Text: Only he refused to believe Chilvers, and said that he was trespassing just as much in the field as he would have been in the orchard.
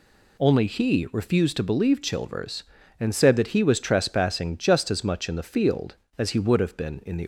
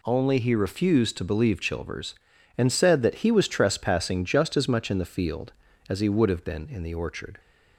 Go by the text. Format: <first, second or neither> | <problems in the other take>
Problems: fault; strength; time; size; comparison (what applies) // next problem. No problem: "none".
second | stops before "orchard"; at 7.2 s